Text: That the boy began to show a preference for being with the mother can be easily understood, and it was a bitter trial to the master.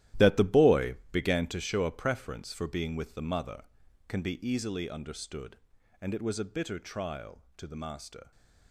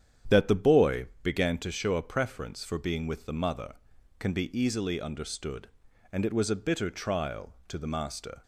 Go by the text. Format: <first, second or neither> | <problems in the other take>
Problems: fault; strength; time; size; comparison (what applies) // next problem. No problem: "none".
second | gets quieter; strong; throughout; 13 dB // starts louder than the rest; strong; until 1.3 s; 14 dB; strong in the second // pauses between "boy" and "began"; slight; at 0.9 s; 0.16 s long; slight in the second